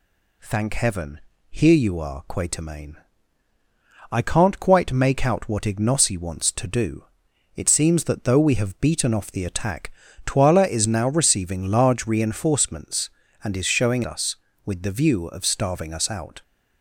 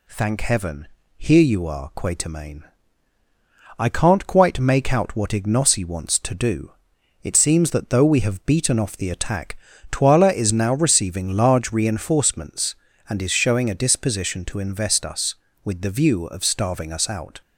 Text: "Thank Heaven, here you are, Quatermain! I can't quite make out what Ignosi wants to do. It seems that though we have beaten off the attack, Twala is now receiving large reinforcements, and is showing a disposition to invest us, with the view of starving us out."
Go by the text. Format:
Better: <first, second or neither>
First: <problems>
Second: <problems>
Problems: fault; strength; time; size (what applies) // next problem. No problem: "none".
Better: second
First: skips "a disposition to invest"; at 14.0 s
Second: none